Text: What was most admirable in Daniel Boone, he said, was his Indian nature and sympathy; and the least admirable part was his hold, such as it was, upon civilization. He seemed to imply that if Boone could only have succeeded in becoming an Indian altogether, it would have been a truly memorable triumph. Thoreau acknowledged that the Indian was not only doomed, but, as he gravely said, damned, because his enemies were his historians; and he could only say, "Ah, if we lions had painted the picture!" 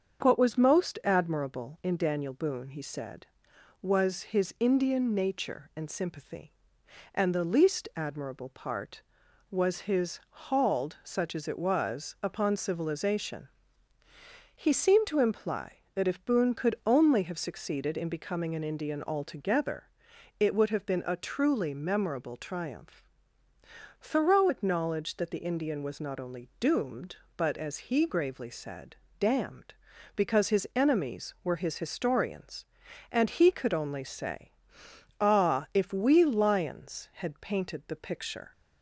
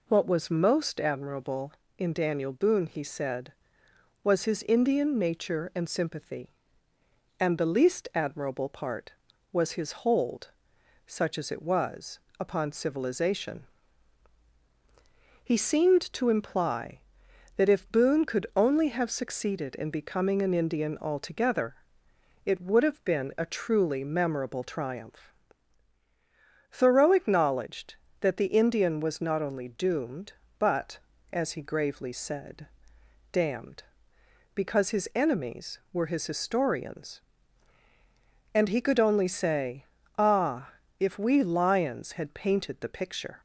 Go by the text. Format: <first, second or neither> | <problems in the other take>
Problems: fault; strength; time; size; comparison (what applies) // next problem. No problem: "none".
second | starts louder than the rest; until 1.2 s; 7 dB // says "hauled" for "hold"; at 10.2 s